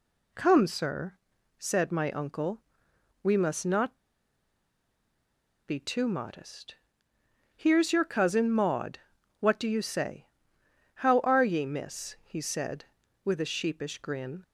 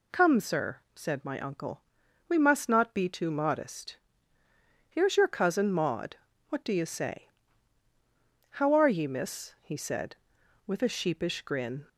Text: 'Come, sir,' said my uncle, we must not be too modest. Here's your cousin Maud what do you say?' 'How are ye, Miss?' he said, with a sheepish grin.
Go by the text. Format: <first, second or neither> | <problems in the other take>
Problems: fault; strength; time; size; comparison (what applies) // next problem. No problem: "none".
second | pauses between "not" and "be"; strong; at 3.9 s; 1.7 s long // pauses between "Maud" and "what"; at 8.9 s; 0.40 s long; slight in the second